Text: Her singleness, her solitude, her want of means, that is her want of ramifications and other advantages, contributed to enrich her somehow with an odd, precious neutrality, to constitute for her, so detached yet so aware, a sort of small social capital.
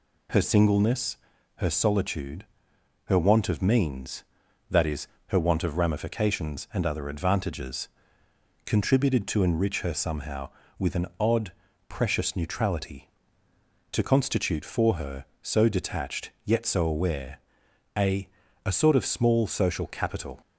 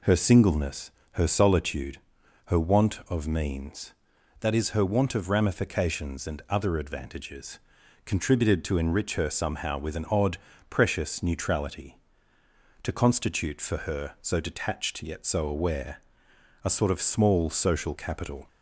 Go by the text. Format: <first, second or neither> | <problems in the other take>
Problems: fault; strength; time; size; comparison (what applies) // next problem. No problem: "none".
second | pauses between "is" and "her"; slight; at 5.0 s; 0.18 s long // says "a" twice; at 18.6 s